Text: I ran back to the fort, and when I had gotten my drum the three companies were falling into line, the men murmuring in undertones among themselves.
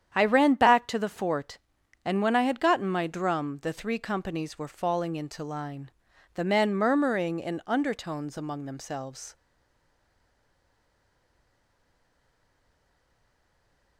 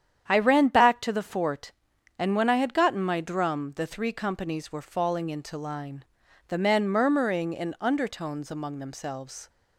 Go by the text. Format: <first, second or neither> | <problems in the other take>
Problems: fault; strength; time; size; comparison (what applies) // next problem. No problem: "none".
second | starts louder than the rest; strong; until 1.1 s; 9 dB; strong in the second // stays silent after the last word; strong; from 9.3 s on; 4.6 s long